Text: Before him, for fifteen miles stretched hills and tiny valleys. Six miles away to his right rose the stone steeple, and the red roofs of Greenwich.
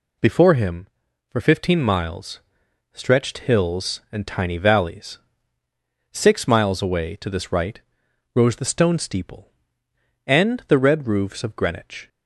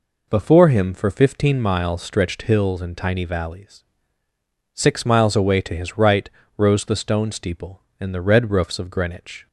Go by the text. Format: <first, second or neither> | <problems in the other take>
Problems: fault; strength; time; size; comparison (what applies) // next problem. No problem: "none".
second | pauses between "miles" and "stretched"; noticeable; at 2.4 s; 0.52 s long // says "this" for "his"; at 7.3 s // pauses between "right" and "rose"; noticeable; at 7.8 s; 0.54 s long; slight in the second